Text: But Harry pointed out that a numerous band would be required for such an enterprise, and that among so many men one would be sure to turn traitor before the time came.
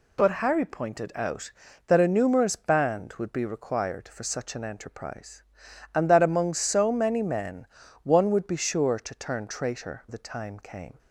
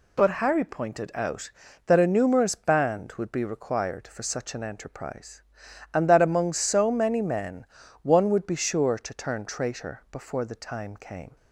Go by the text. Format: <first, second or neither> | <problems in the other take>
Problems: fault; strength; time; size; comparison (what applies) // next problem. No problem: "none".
second | pauses between "men" and "one"; at 7.6 s; 0.38 s long; also in the second // skips "before"; at 10.0 s